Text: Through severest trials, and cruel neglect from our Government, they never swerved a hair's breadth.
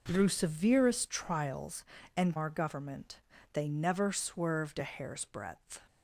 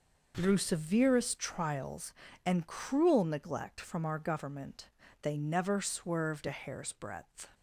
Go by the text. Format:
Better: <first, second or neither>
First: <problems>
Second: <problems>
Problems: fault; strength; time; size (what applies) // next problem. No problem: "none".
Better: second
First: skips "cruel neglect from"; at 2.3 s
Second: none